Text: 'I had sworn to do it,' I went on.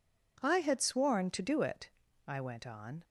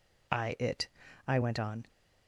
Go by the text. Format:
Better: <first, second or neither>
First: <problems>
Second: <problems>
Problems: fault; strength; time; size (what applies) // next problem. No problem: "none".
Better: first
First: none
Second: skips "had sworn to do"; at 0.5 s